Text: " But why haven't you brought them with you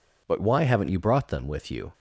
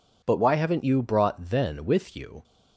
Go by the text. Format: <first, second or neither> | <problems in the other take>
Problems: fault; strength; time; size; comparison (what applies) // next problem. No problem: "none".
first | says "then" for "them"; at 1.4 s